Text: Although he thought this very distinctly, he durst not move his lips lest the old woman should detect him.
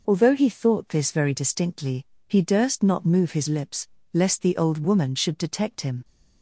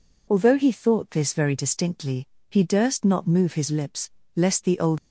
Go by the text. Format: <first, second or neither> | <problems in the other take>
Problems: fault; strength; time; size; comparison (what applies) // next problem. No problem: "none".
first | pauses between "lips" and "lest"; slight; at 4.1 s; 0.24 s long; slight in the first // stops before "woman should detect him"; at 4.9 s